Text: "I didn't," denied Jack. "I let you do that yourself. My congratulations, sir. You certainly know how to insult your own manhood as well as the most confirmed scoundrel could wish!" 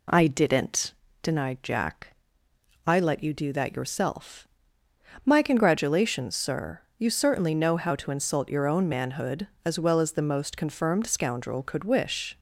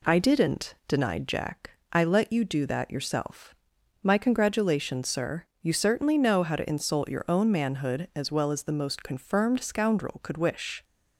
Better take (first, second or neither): neither